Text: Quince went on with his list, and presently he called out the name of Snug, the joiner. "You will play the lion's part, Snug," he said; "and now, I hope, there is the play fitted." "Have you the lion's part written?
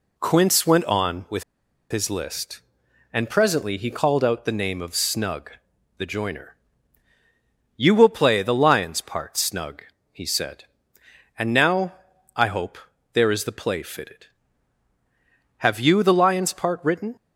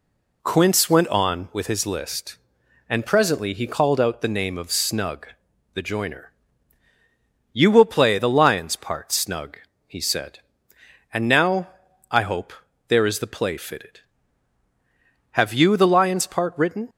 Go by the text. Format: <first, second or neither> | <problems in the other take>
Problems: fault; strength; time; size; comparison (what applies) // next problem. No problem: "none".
second | pauses between "with" and "his"; noticeable; at 1.4 s; 0.47 s long